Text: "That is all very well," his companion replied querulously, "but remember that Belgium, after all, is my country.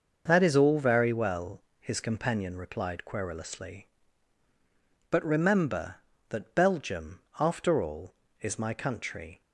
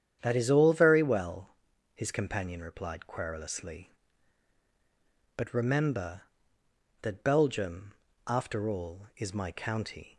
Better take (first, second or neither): first